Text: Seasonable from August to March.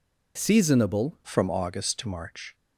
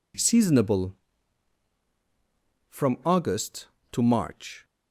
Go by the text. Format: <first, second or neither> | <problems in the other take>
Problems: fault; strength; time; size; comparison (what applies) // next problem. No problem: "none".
second | changes voice at "from"; from 1.2 s on; 1.3 s long